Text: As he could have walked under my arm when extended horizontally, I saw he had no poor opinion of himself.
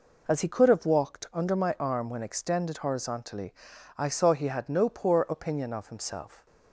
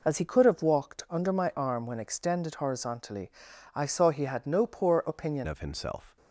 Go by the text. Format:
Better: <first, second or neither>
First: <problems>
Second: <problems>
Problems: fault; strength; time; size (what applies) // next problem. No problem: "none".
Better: first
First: none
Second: changes voice at "of"; from 5.4 s on; 0.7 s long